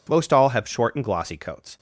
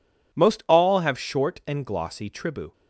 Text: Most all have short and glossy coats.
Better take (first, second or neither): first